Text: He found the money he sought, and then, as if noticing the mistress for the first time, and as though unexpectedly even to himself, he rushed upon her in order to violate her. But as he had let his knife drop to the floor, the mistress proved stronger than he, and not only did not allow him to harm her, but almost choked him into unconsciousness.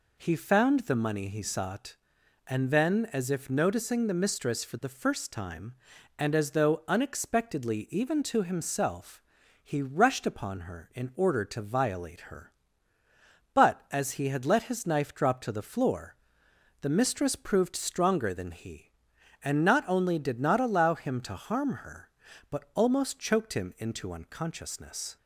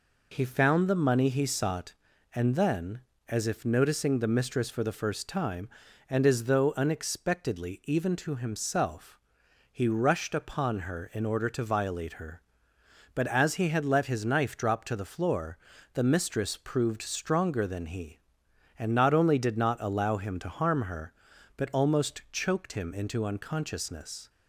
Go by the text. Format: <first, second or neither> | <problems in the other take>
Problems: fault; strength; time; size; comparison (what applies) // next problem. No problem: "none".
neither | none